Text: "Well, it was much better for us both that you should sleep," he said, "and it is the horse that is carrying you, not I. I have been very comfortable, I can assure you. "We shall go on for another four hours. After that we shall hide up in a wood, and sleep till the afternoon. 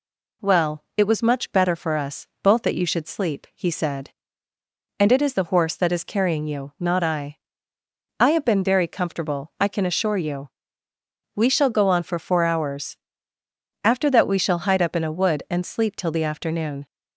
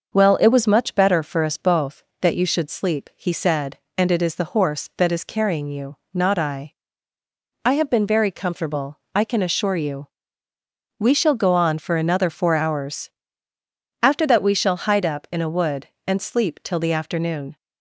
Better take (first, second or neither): second